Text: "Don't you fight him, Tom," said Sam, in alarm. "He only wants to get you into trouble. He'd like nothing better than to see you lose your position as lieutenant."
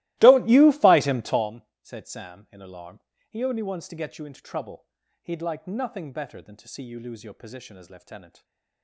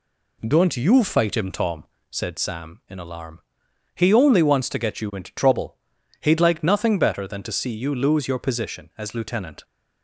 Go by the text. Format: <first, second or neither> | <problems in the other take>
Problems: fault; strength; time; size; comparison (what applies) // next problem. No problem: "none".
second | starts louder than the rest; strong; until 1.6 s; 18 dB // stays silent after the last word; slight; from 8.2 s on; 0.6 s long